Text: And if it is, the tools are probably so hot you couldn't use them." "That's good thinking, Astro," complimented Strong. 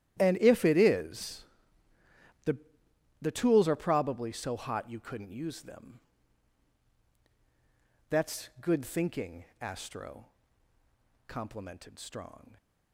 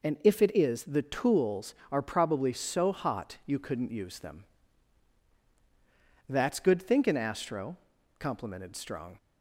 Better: second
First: starts louder than the rest; strong; until 1.2 s; 12 dB // says "the" twice; at 3.2 s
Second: none

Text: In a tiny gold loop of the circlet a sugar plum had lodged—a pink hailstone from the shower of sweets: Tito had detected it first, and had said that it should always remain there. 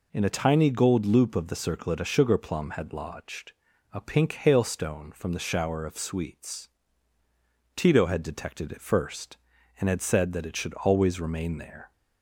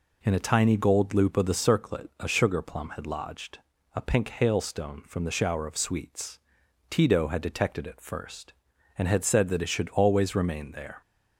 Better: neither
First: none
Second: none

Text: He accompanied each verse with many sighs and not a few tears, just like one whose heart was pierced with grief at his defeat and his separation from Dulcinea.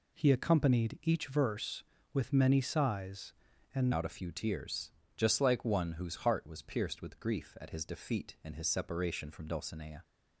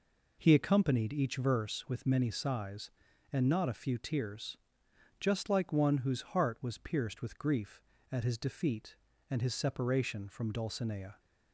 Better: second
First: changes voice at "not"; from 3.9 s on; 6.1 s long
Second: none

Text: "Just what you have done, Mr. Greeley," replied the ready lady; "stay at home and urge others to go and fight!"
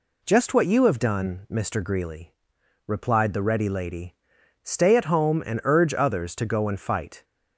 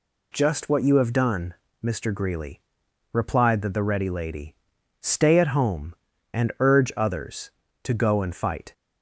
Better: first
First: none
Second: says "the" twice; at 3.6 s

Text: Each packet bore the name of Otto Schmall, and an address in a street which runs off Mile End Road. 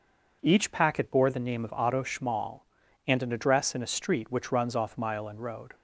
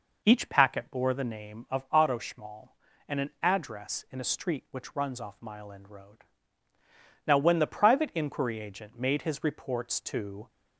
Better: first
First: none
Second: goes on to say "Now when the private inquiry agent made his reports to"; strong; from 7.2 s on; 3.2 s long

